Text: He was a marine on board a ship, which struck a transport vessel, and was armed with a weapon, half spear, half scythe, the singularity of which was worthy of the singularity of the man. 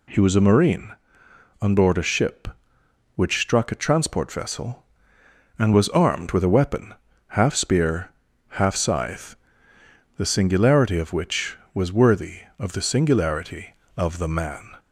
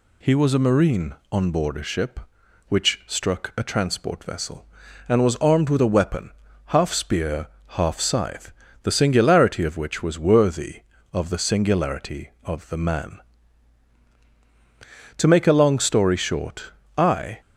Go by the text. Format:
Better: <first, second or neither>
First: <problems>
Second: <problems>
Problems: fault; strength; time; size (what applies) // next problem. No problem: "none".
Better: first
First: none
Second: goes on to say "To make a long story short I"; strong; from 15.1 s on; 2.2 s long